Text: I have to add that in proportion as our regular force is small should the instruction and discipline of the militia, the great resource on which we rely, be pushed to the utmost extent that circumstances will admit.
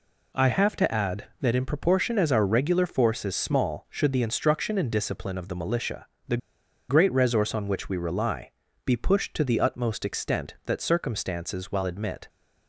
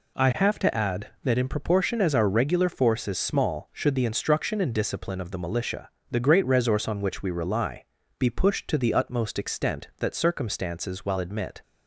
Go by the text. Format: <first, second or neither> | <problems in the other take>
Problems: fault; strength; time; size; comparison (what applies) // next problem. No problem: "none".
second | pauses between "the" and "great"; noticeable; at 6.3 s; 0.52 s long